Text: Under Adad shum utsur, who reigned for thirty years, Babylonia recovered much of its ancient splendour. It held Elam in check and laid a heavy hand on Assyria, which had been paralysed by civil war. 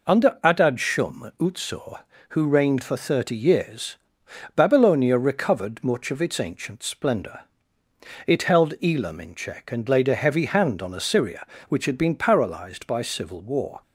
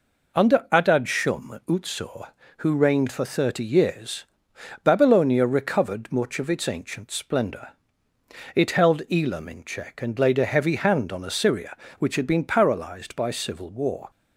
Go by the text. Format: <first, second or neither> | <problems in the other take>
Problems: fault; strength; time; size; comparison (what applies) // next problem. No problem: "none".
neither | none